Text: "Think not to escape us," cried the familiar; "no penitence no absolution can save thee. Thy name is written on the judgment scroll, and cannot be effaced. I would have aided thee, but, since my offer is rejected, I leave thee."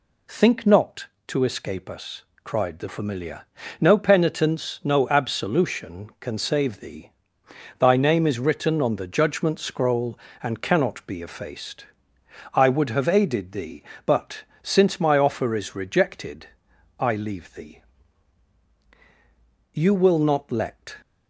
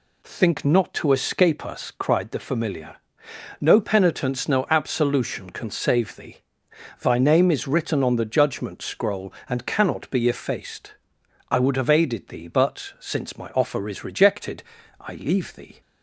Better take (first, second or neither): second